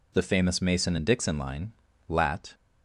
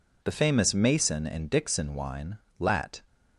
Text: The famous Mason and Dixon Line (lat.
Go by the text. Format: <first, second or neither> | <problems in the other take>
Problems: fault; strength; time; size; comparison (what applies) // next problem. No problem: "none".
first | says "Wine" for "Line"; at 1.9 s